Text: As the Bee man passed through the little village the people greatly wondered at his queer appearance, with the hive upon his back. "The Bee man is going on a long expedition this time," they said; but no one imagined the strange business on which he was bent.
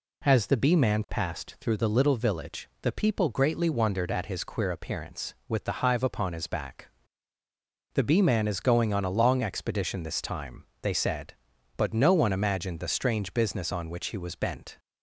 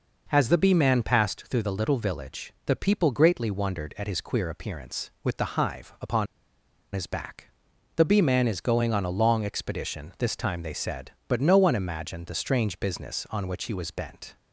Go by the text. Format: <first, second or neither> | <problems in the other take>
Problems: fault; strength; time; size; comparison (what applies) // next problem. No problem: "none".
first | pauses between "upon" and "his"; noticeable; at 6.2 s; 0.68 s long